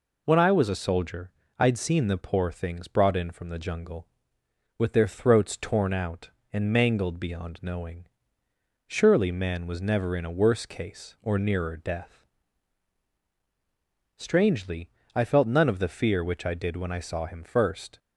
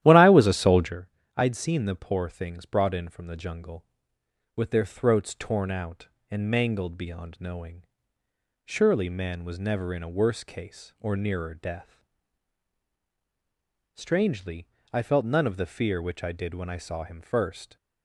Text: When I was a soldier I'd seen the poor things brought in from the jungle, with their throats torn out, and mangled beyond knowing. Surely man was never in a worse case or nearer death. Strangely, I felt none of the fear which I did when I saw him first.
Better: first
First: pauses between "soldier" and "I'd"; slight; at 1.3 s; 0.26 s long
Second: starts louder than the rest; strong; until 1.0 s; 12.5 dB // pauses between "soldier" and "I'd"; slight; at 1.0 s; 0.26 s long

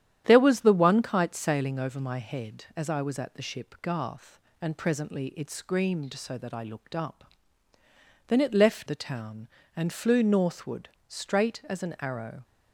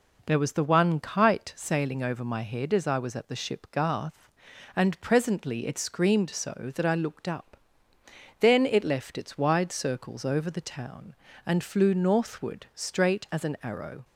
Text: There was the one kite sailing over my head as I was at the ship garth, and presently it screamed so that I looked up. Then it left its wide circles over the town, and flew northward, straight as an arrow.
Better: second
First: starts louder than the rest; strong; until 1.2 s; 10.5 dB // skips "its wide circles over"; at 8.8 s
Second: none

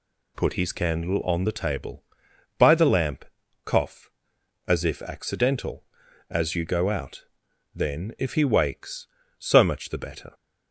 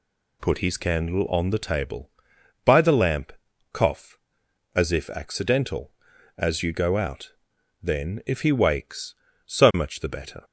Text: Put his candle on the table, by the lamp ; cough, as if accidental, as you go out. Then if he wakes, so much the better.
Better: neither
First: none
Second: none

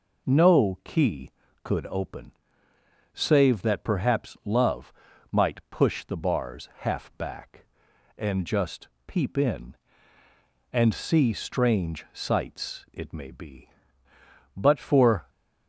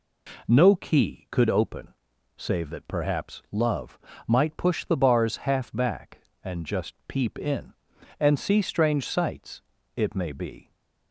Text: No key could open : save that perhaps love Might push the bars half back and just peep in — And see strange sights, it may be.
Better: second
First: pauses between "love" and "Might"; at 4.9 s; 0.40 s long // pauses between "just" and "peep"; slight; at 8.8 s; 0.18 s long // goes on to say "But for"; noticeable; from 14.5 s on; 0.72 s long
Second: pauses between "love" and "Might"; slight; at 3.9 s; 0.30 s long

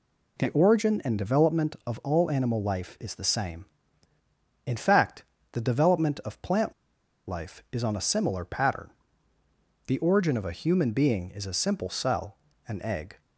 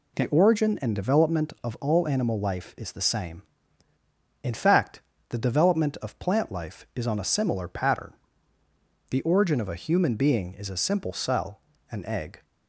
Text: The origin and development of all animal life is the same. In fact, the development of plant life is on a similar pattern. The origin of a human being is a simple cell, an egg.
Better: second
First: pauses between "plant" and "life"; noticeable; at 6.7 s; 0.55 s long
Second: none

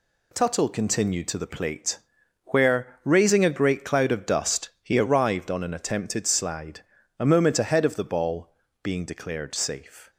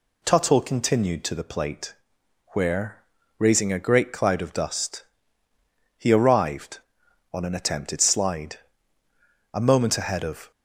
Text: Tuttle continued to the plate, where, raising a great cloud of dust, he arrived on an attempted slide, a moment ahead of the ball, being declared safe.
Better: first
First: none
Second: stops before "the ball being declared safe"; at 10.5 s

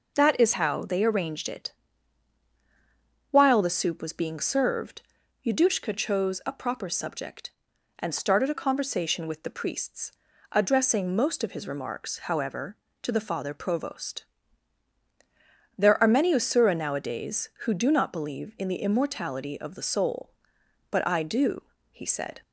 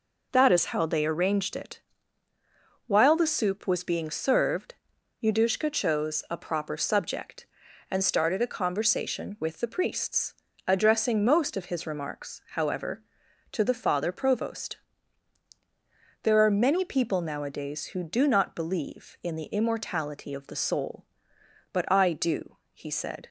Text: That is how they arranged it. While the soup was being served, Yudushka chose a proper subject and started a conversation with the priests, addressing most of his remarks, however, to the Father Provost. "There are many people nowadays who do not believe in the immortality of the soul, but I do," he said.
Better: second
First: says "usura" for "people"; at 16.3 s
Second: none

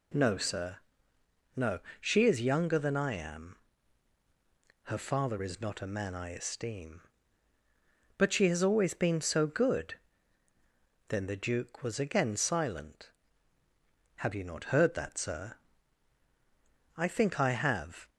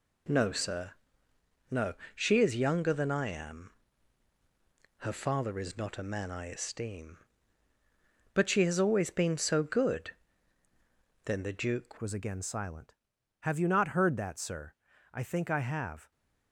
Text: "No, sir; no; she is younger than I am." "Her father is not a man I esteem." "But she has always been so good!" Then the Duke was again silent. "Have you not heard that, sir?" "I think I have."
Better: first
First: none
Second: changes voice at "was"; from 11.9 s on; 4.2 s long

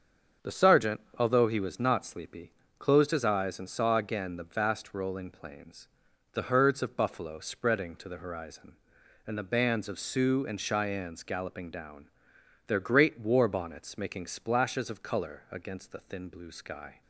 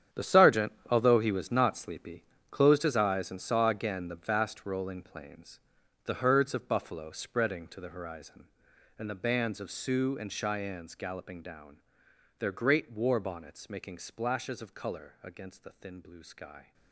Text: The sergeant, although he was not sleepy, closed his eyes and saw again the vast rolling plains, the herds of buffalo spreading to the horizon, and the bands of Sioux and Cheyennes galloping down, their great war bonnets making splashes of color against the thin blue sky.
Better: first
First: starts louder than the rest; until 1.5 s; 6.5 dB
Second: gets quieter; strong; throughout; 13.5 dB // starts louder than the rest; strong; until 1.3 s; 9 dB

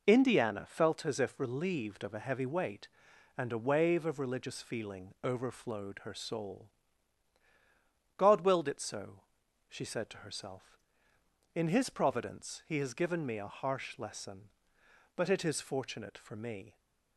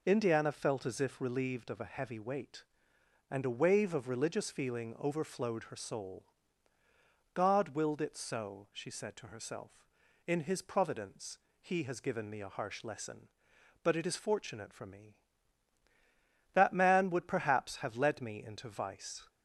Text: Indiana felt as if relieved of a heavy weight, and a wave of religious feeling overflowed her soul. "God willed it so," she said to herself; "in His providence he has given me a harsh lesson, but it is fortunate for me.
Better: first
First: none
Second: pauses between "providence" and "he"; slight; at 11.3 s; 0.22 s long // goes on to say "That man would perhaps have led me into vice"; strong; from 16.5 s on; 2.7 s long

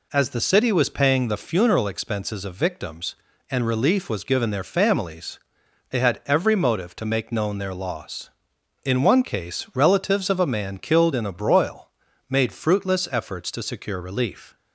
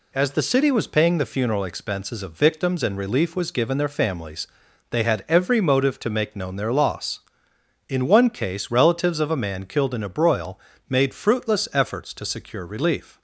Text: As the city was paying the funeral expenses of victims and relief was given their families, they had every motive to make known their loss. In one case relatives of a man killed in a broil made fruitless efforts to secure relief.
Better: neither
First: pauses between "broil" and "made"; at 11.8 s; 0.40 s long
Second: pauses between "broil" and "made"; slight; at 10.5 s; 0.30 s long

